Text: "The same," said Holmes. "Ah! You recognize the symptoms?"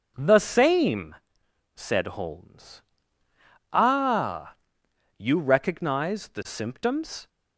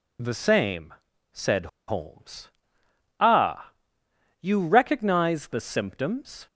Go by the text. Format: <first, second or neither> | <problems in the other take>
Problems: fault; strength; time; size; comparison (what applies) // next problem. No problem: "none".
first | pauses between "said" and "Holmes"; slight; at 1.6 s; 0.21 s long